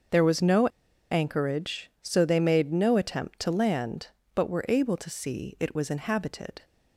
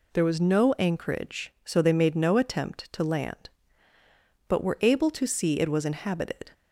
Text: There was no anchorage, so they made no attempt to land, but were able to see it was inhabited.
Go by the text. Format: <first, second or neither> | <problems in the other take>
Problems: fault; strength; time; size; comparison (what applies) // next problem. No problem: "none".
second | starts louder than the rest; until 1.5 s; 6.5 dB // pauses between "no" and "anchorage"; at 0.6 s; 0.43 s long